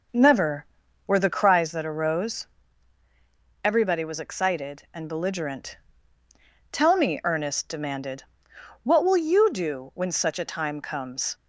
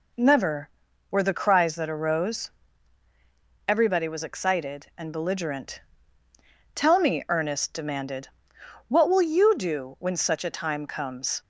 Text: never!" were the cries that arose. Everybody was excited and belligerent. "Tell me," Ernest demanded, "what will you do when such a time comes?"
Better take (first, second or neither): second